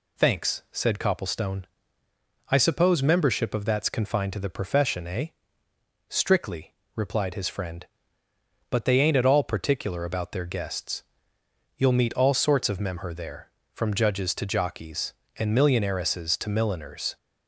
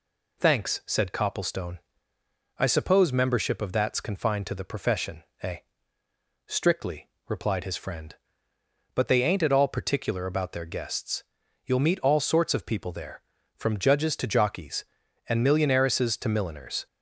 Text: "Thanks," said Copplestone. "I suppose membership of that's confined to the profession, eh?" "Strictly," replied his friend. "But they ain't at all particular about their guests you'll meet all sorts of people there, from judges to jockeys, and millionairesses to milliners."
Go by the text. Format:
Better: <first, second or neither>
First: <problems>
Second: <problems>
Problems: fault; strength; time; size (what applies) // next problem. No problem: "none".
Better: second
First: pauses between "guests" and "you'll"; noticeable; at 11.0 s; 0.76 s long // says "memher" for "people"; at 12.7 s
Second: pauses between "guests" and "you'll"; at 11.2 s; 0.42 s long